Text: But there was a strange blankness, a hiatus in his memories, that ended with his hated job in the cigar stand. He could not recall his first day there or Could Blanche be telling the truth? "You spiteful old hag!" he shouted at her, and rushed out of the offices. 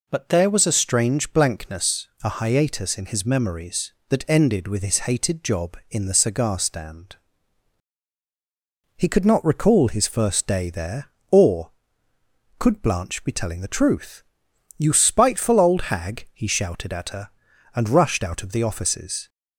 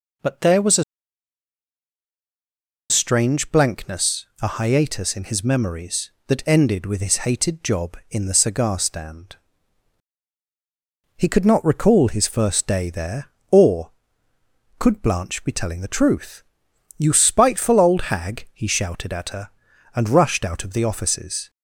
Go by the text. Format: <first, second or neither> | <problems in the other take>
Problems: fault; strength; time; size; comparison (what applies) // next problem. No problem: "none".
first | pauses between "a" and "strange"; strong; at 0.8 s; 2.0 s long